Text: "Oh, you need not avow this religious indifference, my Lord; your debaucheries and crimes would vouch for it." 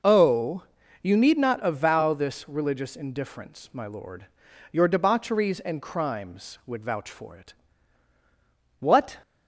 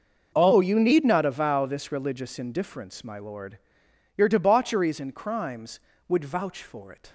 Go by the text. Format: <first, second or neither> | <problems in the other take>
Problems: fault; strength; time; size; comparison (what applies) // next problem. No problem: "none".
second | goes on to say "What"; slight; from 8.7 s on; 0.40 s long